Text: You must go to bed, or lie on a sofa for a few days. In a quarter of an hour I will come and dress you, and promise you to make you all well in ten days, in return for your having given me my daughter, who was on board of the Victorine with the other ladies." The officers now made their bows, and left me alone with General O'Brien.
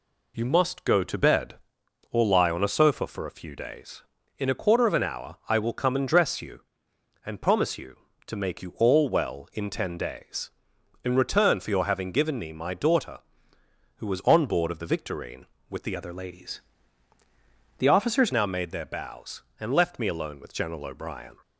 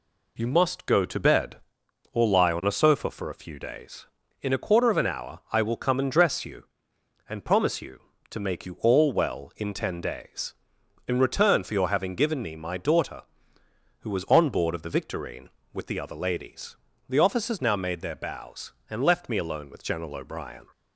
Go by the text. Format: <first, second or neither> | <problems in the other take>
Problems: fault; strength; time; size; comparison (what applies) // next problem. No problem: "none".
second | changes voice from "other" to "officers"; from 15.9 to 18.3 s; 2.4 s long